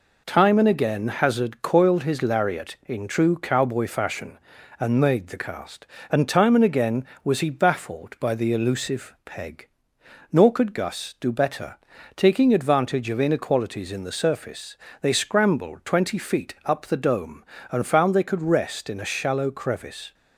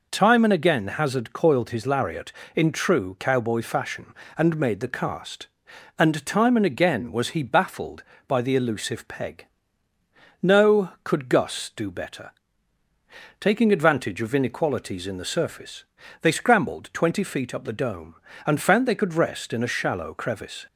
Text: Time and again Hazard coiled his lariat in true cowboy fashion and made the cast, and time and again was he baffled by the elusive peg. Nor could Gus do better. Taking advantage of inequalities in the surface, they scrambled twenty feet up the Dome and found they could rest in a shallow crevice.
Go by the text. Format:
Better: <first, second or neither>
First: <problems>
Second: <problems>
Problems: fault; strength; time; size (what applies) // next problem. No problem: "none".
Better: first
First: none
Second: says "No" for "Nor"; at 10.4 s